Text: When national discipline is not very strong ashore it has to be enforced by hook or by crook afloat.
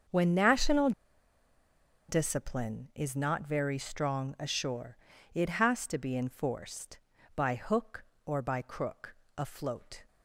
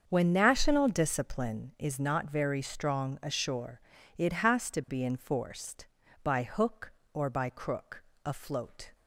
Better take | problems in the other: second | starts louder than the rest; until 2.2 s; 7 dB; also in the second // pauses between "national" and "discipline"; at 0.9 s; 1.1 s long // pauses between "ashore" and "it"; at 4.9 s; 0.38 s long; also in the second // pauses between "crook" and "afloat"; slight; at 9.1 s; 0.24 s long; slight in the second

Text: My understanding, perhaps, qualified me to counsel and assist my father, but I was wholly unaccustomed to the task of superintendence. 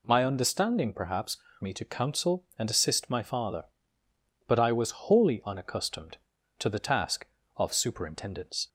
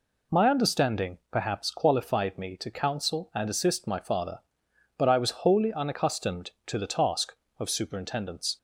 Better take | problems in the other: second | skips "qualified"; at 1.4 s

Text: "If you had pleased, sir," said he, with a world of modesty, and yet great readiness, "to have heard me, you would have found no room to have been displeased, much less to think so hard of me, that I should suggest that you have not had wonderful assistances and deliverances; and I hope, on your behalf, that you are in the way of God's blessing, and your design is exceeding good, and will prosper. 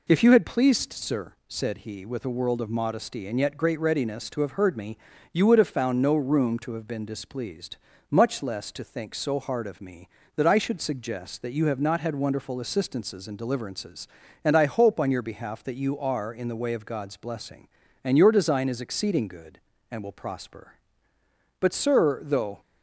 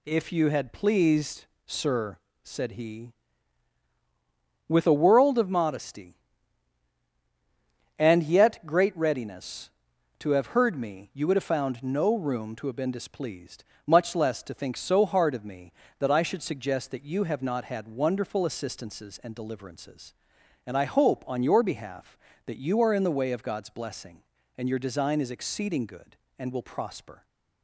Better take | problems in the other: second | goes on to say "But sir though"; noticeable; from 21.5 s on; 1.0 s long

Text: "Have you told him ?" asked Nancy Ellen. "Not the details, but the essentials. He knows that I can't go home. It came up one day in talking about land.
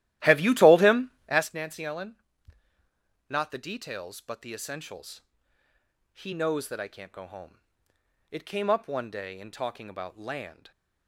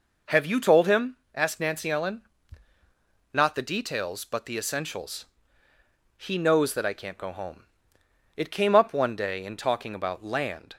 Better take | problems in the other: second | starts louder than the rest; strong; until 1.5 s; 14.5 dB

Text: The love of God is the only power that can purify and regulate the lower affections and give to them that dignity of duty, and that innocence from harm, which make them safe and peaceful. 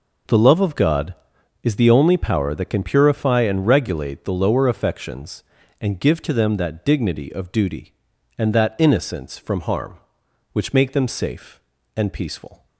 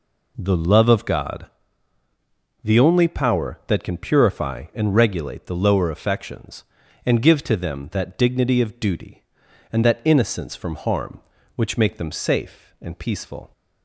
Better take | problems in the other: first | skips "is"; at 2.0 s

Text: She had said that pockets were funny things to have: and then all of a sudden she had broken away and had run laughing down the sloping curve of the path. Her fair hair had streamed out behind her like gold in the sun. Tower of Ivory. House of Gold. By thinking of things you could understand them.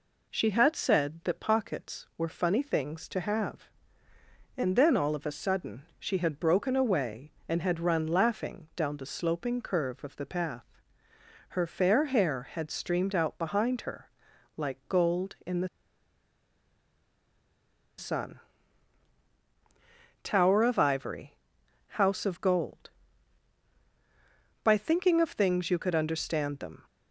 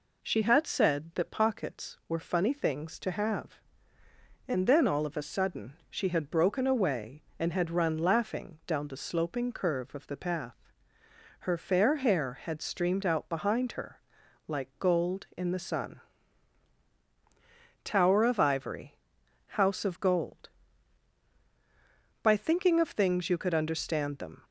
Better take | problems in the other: second | pauses between "her" and "like"; noticeable; at 14.0 s; 0.48 s long; noticeable in the second // pauses between "the" and "sun"; strong; at 15.6 s; 2.3 s long

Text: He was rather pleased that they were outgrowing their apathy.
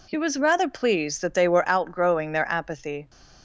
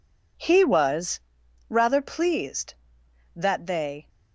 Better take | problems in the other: first | pauses between "was" and "rather"; noticeable; at 1.2 s; 0.48 s long // stops before "were outgrowing their apathy"; at 4.0 s

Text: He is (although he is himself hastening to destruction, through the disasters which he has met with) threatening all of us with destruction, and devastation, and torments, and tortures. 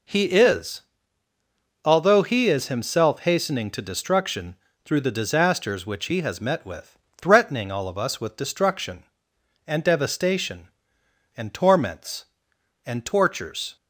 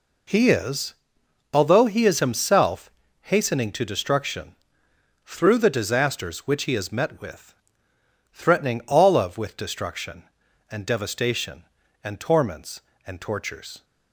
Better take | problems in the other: first | pauses between "himself" and "hastening"; at 2.9 s; 0.42 s long // skips "us"; at 9.3 s

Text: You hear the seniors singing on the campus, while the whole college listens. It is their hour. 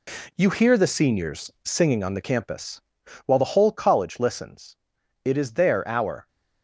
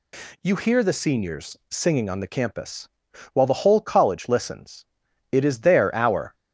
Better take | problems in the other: second | gets quieter; strong; throughout; 7 dB

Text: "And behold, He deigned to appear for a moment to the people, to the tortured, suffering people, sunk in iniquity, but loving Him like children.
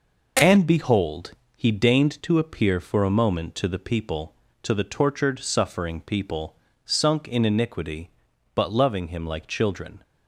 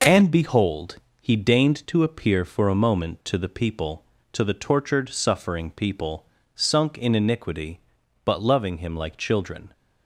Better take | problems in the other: neither | none

